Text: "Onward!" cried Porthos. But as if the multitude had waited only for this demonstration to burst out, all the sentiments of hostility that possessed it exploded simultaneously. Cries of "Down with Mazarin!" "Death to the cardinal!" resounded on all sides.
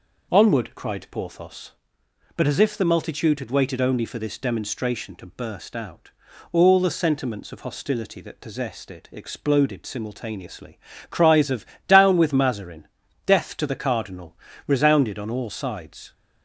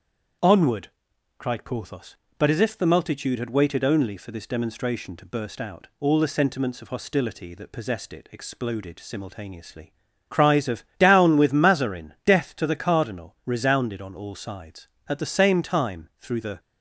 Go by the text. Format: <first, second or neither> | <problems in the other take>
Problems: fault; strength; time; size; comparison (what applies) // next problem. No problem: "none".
first | starts louder than the rest; strong; until 1.9 s; 7.5 dB // pauses between "of" and "Down"; slight; at 10.8 s; 0.16 s long; slight in the first // goes on to say "At the same time through the"; from 15.0 s on; 1.5 s long